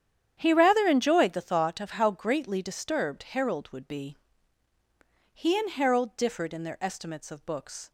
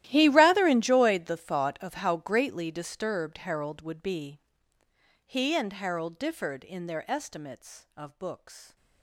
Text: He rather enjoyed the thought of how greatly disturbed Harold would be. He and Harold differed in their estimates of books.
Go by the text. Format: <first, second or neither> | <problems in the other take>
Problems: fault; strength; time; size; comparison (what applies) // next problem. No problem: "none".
first | gets quieter; strong; throughout; 20.5 dB // starts louder than the rest; strong; until 1.0 s; 14 dB; strong in the first